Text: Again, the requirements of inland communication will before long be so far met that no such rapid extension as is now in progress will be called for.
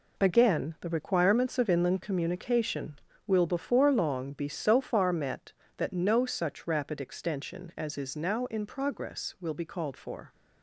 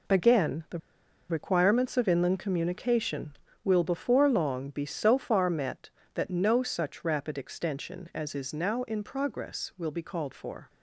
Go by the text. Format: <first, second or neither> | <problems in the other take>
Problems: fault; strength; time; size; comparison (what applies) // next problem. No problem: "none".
first | pauses between "the" and "requirements"; noticeable; at 0.7 s; 0.52 s long